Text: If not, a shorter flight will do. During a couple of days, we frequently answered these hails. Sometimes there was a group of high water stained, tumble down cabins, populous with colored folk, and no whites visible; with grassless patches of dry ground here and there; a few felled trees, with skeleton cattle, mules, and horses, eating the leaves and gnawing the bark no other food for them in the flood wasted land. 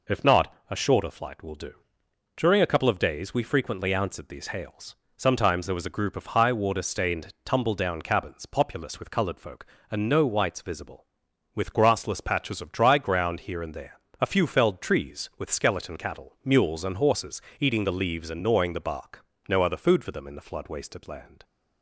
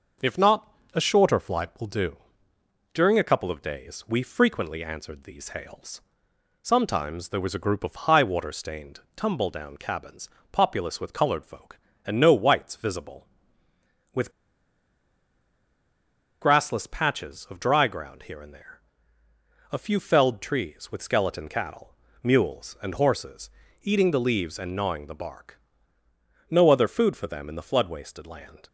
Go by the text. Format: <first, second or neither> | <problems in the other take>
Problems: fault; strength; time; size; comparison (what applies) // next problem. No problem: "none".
first | pauses between "with" and "grassless"; strong; at 14.3 s; 2.1 s long // pauses between "bark" and "no"; noticeable; at 25.6 s; 0.90 s long; slight in the first